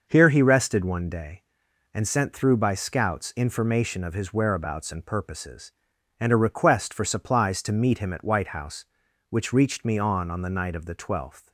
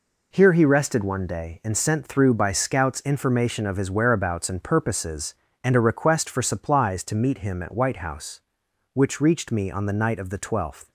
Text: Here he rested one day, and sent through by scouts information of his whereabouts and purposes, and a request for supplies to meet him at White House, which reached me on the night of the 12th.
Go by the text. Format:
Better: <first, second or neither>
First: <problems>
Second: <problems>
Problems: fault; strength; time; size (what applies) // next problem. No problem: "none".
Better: second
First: starts louder than the rest; noticeable; until 1.1 s; 6 dB // says "on" twice; at 10.3 s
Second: none